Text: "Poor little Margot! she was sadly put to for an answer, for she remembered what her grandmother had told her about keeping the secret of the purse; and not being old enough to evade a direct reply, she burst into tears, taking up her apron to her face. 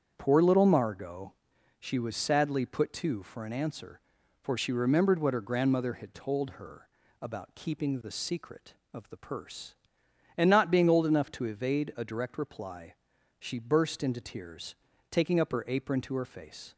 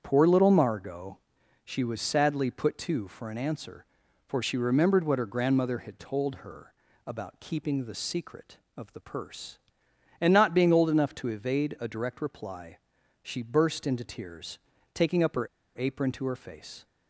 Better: first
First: starts louder than the rest; strong; until 1.1 s; 8 dB // pauses between "her" and "about"; slight; at 6.8 s; 0.32 s long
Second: starts louder than the rest; strong; until 1.0 s; 8 dB // pauses between "her" and "about"; slight; at 6.7 s; 0.32 s long // pauses between "her" and "apron"; slight; at 15.4 s; 0.29 s long

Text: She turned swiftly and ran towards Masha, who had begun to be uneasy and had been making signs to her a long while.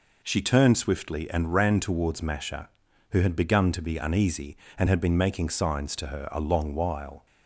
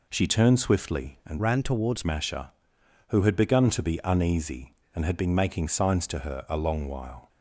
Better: first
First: none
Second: changes voice from "ran" to "towards"; from 1.3 to 2.0 s; 0.7 s long

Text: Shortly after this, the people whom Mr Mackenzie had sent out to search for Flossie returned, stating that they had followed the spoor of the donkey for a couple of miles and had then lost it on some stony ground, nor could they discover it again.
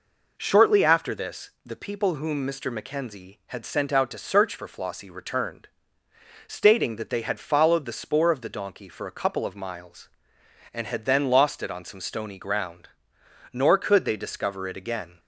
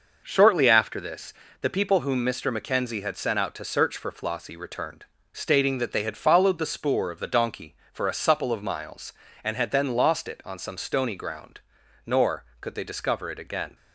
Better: first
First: none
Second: says "supple" for "couple"; at 8.1 s

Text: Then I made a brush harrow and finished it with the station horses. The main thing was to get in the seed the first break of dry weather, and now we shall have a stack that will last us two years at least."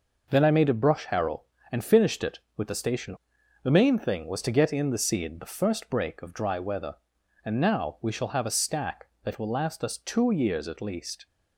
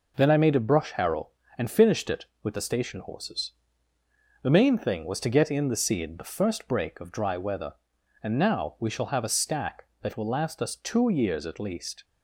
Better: second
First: skips "horses"; at 3.3 s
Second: none

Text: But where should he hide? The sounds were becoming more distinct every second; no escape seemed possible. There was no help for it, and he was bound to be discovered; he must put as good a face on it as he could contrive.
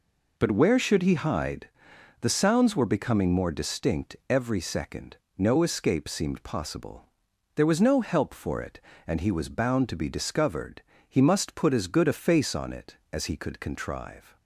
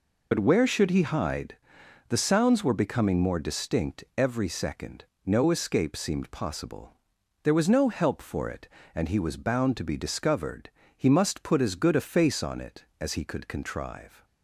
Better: first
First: none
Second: loses the start of "But"; at 0.3 s; 50 ms

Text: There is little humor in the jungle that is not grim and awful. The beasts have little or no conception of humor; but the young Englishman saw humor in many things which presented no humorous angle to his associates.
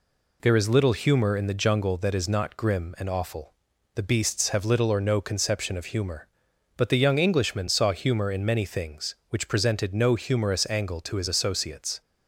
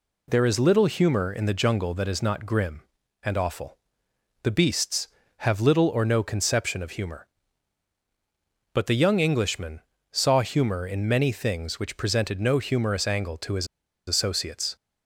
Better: first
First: none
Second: pauses between "Englishman" and "saw"; slight; at 9.8 s; 0.30 s long // pauses between "his" and "associates"; at 13.6 s; 0.42 s long

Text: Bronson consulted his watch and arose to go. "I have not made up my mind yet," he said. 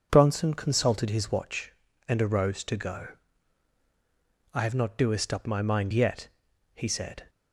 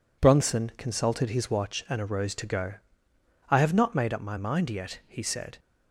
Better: second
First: says "doest" for "made"; at 4.9 s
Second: none

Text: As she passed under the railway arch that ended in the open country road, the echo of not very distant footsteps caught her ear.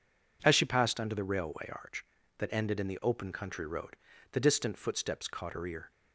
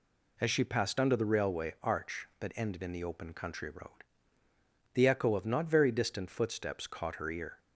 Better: second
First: skips "echo of not very"; at 4.4 s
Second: none

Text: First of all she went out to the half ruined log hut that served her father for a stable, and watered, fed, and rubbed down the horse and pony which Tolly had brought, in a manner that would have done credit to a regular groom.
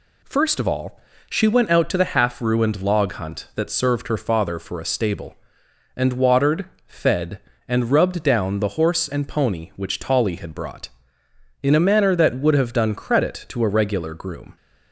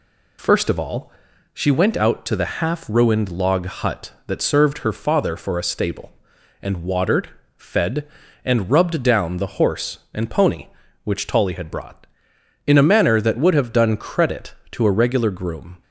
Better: second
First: pauses between "all" and "she"; slight; at 0.9 s; 0.30 s long // says "hunt" for "hut"; at 3.1 s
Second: pauses between "all" and "she"; at 1.1 s; 0.40 s long

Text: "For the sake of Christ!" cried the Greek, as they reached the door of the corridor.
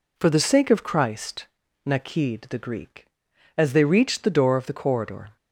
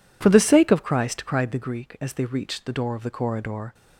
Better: second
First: says "nakid" for "cried"; at 1.8 s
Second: none

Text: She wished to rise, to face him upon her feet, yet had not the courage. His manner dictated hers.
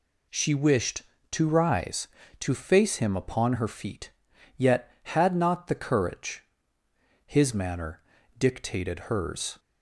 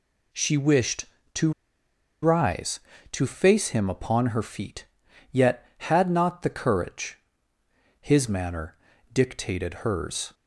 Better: first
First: pauses between "manner" and "dictated"; slight; at 8.0 s; 0.36 s long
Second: pauses between "to" and "rise"; noticeable; at 1.5 s; 0.71 s long // pauses between "manner" and "dictated"; slight; at 8.7 s; 0.36 s long

